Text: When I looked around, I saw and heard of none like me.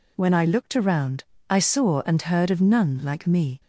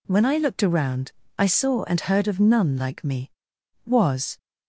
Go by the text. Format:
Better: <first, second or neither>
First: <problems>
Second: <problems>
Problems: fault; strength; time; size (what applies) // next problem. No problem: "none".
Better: first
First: none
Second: goes on to say "Was"; from 3.8 s on; 0.50 s long